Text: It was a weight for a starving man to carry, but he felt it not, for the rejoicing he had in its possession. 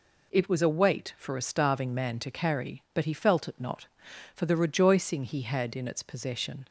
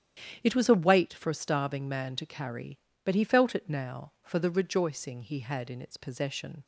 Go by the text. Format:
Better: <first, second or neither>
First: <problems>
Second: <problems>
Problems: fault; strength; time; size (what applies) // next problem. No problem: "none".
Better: first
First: none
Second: starts louder than the rest; strong; until 1.4 s; 9.5 dB // says "now" for "not"; at 3.6 s